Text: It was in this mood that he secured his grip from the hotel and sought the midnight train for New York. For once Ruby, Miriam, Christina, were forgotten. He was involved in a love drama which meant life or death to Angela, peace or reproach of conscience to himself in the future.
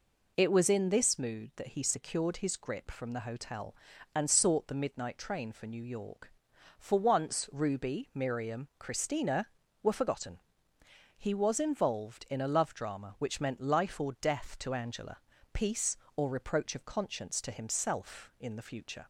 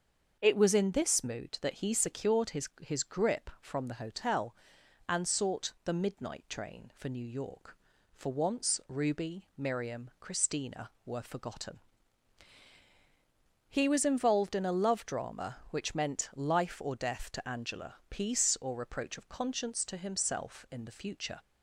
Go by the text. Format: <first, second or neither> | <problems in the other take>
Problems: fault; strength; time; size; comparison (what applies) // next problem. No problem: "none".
first | starts louder than the rest; until 1.4 s; 6.5 dB // says "his" twice; at 2.7 s